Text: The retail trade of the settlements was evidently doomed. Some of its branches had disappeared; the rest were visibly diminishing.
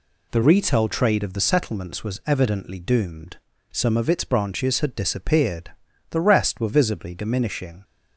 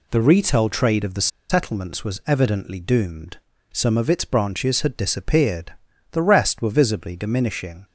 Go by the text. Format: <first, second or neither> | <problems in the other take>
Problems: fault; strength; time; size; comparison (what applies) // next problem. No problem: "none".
first | pauses between "the" and "settlements"; slight; at 1.2 s; 0.22 s long